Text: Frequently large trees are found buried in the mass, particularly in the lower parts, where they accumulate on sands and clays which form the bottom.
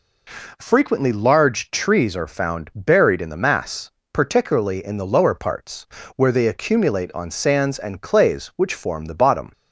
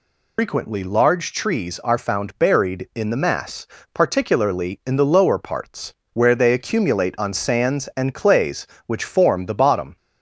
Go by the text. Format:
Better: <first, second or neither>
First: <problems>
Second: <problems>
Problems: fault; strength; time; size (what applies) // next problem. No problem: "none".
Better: first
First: none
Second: loses the start of "Frequently"; at 0.3 s; 120 ms